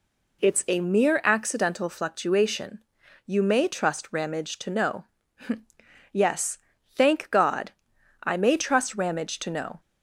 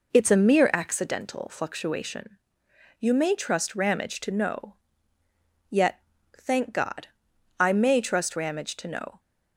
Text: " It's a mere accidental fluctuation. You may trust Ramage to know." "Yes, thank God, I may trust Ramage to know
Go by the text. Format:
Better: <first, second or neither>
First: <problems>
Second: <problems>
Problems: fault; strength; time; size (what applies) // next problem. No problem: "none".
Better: first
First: none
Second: says "Yet" for "Yes"; at 5.6 s